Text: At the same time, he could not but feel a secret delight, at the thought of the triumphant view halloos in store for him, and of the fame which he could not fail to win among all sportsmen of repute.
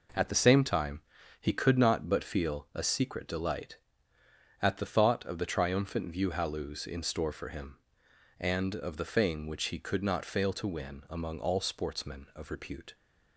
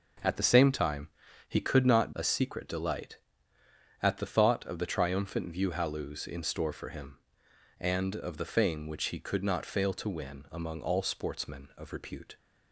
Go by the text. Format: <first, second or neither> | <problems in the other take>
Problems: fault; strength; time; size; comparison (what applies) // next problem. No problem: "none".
first | skips "but feel"; at 2.1 s